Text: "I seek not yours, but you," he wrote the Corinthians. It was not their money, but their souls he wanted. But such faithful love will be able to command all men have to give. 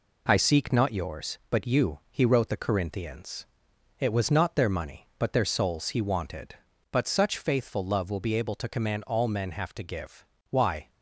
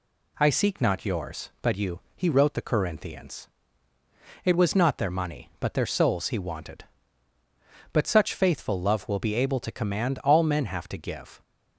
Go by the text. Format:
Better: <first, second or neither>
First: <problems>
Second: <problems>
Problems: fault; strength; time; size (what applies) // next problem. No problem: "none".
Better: second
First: goes on to say "Why"; slight; from 10.5 s on; 0.38 s long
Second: none